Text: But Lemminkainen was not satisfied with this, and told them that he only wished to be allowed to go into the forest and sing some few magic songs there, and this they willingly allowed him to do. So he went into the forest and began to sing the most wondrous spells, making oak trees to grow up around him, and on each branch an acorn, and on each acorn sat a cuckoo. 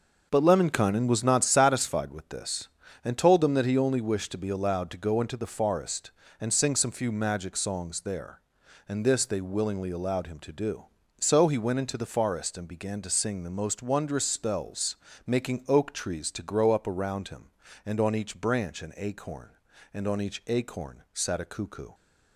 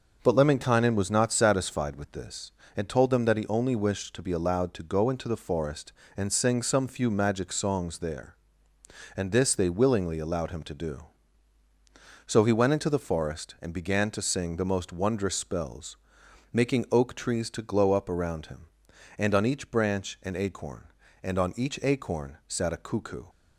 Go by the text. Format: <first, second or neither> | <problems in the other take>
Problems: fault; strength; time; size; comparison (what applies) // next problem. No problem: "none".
first | starts louder than the rest; noticeable; until 1.2 s; 6 dB; noticeable in the first // says "glow" for "grow"; at 17.6 s